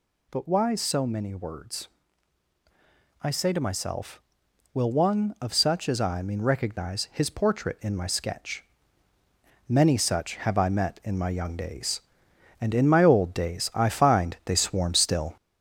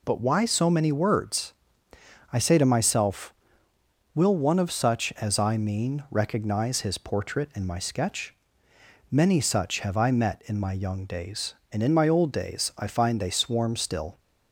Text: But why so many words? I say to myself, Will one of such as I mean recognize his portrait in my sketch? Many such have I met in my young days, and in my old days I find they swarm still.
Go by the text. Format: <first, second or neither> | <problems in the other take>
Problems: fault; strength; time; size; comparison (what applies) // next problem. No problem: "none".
second | gets louder; throughout; 4 dB